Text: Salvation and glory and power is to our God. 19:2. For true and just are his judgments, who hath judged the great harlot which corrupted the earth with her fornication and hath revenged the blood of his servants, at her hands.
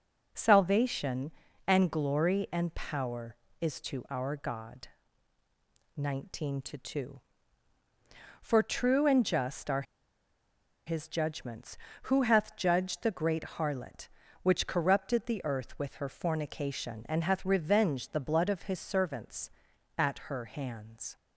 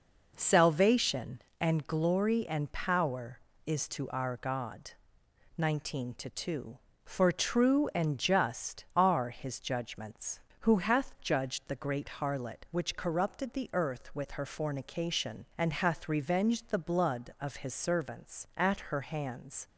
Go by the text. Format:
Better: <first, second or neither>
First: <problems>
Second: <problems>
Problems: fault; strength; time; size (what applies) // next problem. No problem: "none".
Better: second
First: pauses between "are" and "his"; at 9.8 s; 1.0 s long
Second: none